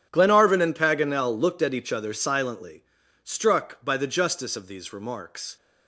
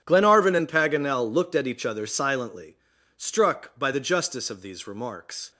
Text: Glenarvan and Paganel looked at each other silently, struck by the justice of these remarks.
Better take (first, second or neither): neither